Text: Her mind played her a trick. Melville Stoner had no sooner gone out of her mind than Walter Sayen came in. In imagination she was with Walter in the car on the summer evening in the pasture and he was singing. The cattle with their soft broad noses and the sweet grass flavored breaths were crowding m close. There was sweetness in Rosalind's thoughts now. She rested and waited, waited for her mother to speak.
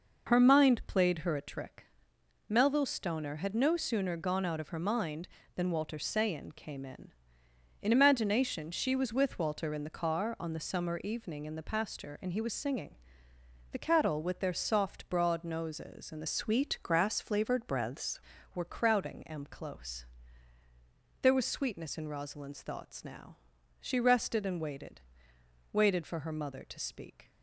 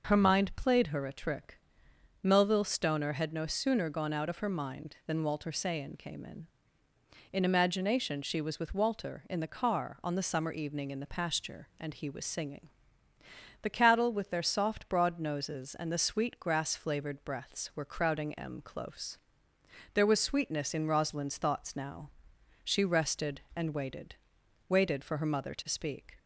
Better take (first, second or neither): second